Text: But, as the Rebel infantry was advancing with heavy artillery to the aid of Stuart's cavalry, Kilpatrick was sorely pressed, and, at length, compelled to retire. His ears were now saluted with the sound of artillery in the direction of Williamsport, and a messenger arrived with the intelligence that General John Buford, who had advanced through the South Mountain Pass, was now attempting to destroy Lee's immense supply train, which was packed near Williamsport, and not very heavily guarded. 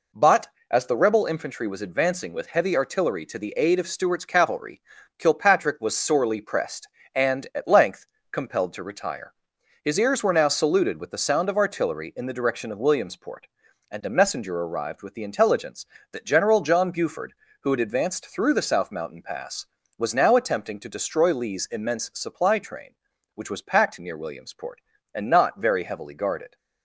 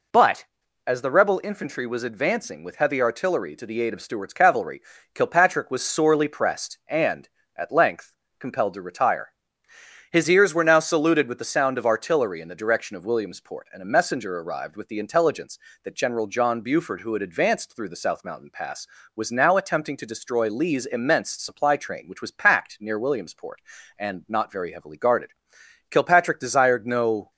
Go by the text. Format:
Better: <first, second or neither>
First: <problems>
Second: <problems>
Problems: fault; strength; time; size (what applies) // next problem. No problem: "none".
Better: first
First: none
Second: goes on to say "Kilpatrick desired no"; from 25.8 s on; 1.4 s long